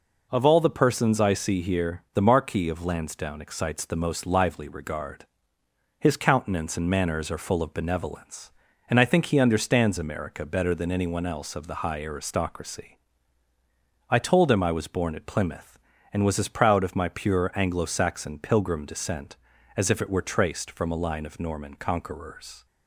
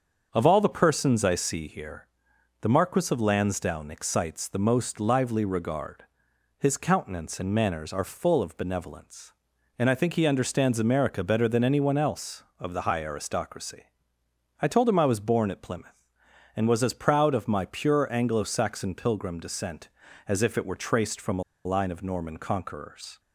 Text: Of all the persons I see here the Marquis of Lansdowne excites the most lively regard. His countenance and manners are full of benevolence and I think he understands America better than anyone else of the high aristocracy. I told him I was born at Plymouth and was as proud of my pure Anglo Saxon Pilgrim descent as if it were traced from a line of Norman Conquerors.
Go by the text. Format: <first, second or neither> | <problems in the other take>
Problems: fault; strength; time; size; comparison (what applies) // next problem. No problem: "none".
first | starts louder than the rest; until 1.3 s; 7 dB // pauses between "here" and "the"; noticeable; at 2.0 s; 0.56 s long // pauses between "a" and "line"; slight; at 21.4 s; 0.22 s long